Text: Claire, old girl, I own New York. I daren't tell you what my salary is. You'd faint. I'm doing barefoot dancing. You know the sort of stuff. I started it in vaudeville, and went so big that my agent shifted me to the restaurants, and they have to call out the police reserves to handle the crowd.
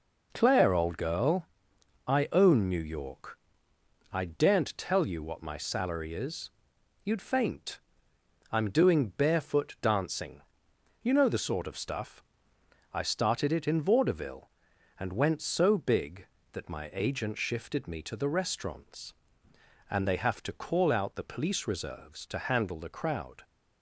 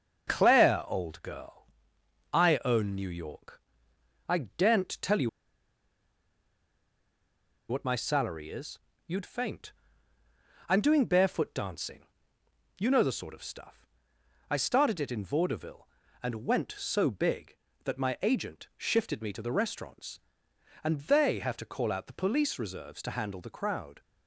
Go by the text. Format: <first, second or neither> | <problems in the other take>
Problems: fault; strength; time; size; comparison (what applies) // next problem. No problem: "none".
first | starts louder than the rest; until 1.3 s; 6.5 dB // pauses between "you" and "what"; strong; at 5.2 s; 2.4 s long